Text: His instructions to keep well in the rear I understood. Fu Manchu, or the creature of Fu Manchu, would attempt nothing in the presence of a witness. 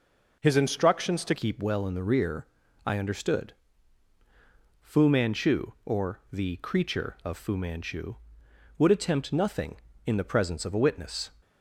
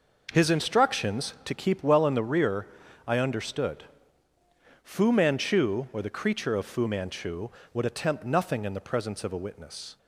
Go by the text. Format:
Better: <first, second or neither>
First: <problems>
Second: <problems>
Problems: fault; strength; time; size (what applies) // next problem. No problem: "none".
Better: second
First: changes voice at "keep"; from 1.3 s on; 10.0 s long // pauses between "rear" and "I"; at 2.4 s; 0.38 s long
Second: pauses between "rear" and "I"; at 2.6 s; 0.40 s long